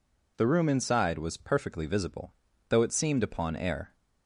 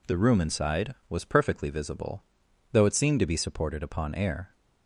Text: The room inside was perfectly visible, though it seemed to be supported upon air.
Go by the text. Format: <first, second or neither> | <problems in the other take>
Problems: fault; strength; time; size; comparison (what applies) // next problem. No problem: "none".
second | skips "to be supported"; at 3.2 s